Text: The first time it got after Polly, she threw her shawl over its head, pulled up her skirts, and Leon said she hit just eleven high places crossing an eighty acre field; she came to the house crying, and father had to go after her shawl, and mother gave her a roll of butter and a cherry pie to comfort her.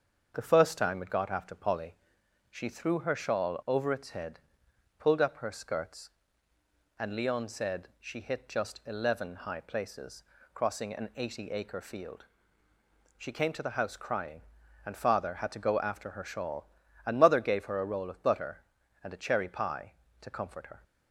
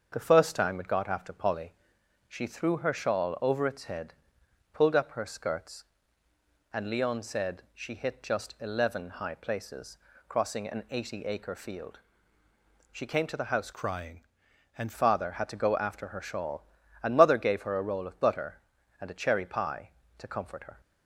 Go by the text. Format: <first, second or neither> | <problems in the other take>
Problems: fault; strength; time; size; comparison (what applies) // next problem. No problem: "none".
first | starts louder than the rest; until 1.1 s; 7 dB; also in the first // pauses between "places" and "crossing"; slight; at 9.9 s; 0.30 s long; slight in the first // changes voice from "crying" to "and"; from 13.7 to 14.9 s; 1.2 s long